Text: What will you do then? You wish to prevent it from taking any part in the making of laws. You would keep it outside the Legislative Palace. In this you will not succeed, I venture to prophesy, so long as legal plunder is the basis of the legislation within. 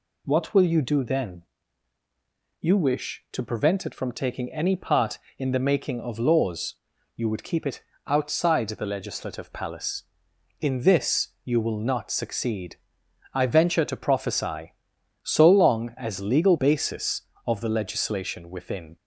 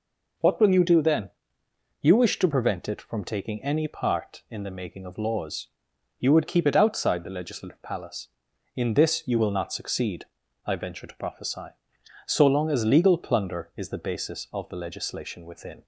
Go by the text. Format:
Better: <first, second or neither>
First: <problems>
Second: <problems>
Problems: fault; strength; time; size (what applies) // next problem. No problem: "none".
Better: second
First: pauses between "it" and "outside"; slight; at 7.8 s; 0.26 s long // pauses between "this" and "you"; slight; at 11.2 s; 0.16 s long // skips "plunder is the"; at 16.5 s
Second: none